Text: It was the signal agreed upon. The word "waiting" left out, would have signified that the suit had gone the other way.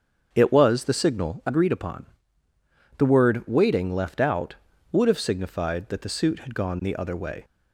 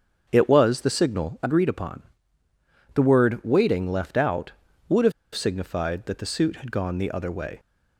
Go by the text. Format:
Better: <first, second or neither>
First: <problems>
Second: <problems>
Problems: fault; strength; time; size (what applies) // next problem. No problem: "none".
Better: first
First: starts louder than the rest; until 1.3 s; 7 dB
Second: starts louder than the rest; until 1.3 s; 7 dB // pauses between "have" and "signified"; slight; at 5.1 s; 0.23 s long